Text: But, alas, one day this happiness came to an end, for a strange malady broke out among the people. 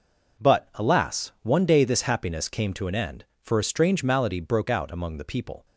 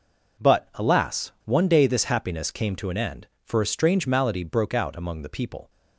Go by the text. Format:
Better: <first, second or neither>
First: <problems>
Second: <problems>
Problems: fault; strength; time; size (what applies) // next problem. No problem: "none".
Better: neither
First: none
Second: none